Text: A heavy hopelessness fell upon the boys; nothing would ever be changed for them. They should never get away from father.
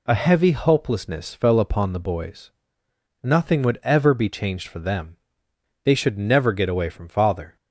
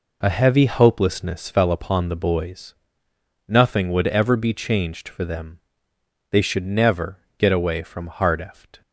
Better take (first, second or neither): first